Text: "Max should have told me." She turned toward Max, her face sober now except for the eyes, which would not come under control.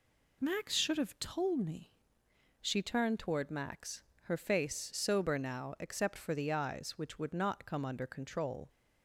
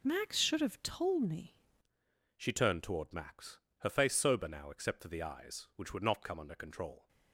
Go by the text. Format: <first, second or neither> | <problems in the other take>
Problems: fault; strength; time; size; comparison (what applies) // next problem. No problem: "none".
first | changes voice at "She"; from 2.3 s on; 4.7 s long